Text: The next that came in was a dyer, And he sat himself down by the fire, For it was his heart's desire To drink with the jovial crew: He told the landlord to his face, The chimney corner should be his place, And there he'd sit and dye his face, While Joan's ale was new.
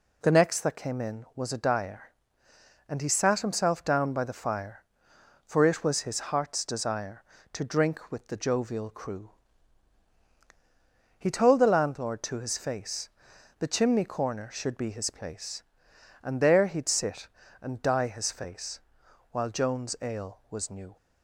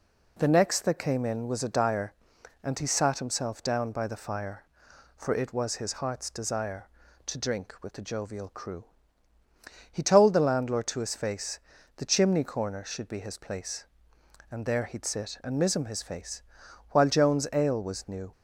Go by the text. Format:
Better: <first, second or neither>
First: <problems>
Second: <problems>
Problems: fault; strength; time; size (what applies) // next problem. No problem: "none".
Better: first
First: none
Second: says "mism" for "dye"; at 15.5 s